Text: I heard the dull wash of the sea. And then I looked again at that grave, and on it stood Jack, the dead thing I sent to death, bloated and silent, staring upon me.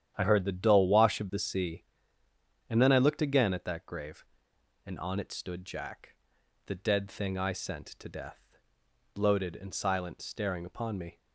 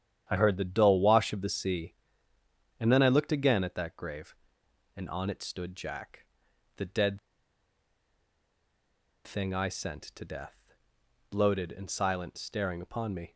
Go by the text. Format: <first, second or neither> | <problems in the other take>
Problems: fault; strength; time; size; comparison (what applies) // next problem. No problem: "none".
first | starts louder than the rest; strong; until 1.3 s; 9.5 dB; strong in the first // pauses between "dead" and "thing"; strong; at 7.1 s; 2.0 s long